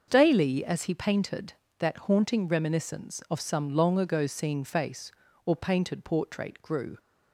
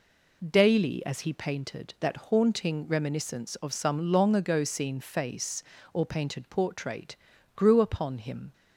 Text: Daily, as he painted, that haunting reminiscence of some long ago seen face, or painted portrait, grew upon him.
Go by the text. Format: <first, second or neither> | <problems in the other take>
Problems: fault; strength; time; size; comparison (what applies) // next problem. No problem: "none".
second | starts louder than the rest; until 1.0 s; 6 dB // stops before "upon him"; at 6.9 s